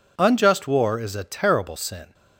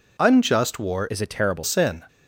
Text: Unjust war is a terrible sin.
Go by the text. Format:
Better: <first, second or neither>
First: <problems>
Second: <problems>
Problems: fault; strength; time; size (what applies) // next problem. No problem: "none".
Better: first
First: none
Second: changes voice from "is" to "terrible"; from 1.0 to 1.6 s; 0.6 s long